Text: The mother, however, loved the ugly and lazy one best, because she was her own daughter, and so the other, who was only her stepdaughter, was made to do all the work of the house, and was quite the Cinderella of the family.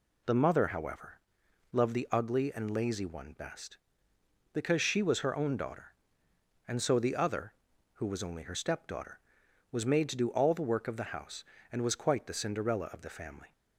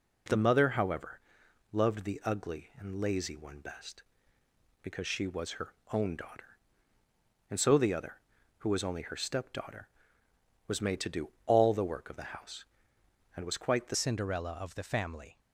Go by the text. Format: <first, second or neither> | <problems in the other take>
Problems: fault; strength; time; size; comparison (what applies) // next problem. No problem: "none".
first | pauses between "her" and "own"; slight; at 5.6 s; 0.24 s long // pauses between "do" and "all"; slight; at 11.2 s; 0.16 s long // changes voice at "Cinderella"; from 13.9 s on; 1.4 s long